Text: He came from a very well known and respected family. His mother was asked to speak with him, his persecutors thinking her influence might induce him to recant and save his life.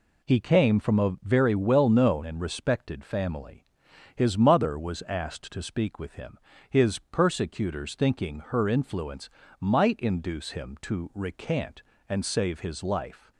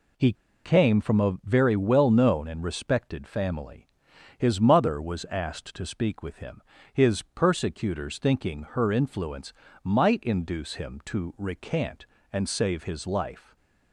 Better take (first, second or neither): first